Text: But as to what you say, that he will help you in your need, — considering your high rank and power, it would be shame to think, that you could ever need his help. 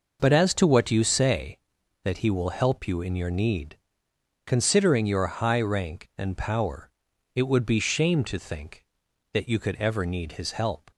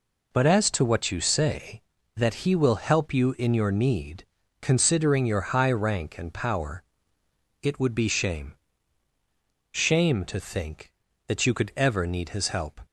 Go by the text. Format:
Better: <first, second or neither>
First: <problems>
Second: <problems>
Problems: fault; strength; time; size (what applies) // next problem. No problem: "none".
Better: first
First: none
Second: says "shame" twice; at 9.7 s